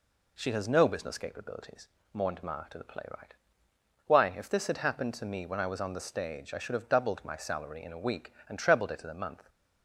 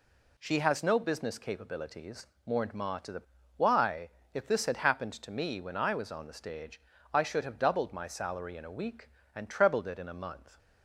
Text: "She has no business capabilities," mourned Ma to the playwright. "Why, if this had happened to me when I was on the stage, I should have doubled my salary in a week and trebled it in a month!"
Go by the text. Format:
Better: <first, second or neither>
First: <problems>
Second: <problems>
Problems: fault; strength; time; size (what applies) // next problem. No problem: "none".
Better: first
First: none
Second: skips "playwright"; at 3.4 s